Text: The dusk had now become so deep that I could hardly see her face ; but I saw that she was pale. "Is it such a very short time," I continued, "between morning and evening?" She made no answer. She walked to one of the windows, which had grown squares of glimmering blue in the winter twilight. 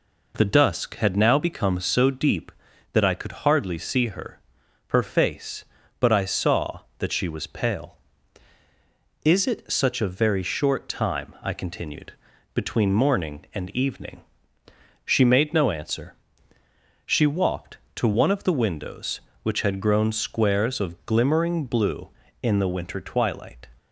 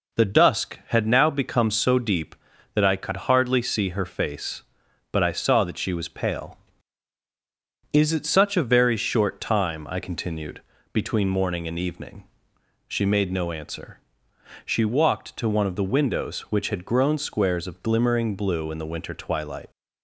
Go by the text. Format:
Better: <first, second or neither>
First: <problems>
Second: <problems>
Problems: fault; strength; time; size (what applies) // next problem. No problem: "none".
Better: second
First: says "her" twice; at 4.8 s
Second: none